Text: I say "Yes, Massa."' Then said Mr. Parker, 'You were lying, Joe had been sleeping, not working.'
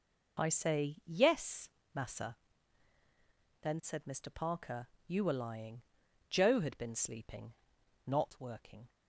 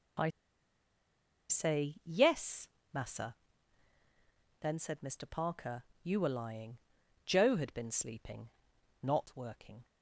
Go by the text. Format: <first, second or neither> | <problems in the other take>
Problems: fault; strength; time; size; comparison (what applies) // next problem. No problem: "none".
first | pauses between "I" and "say"; at 0.2 s; 1.2 s long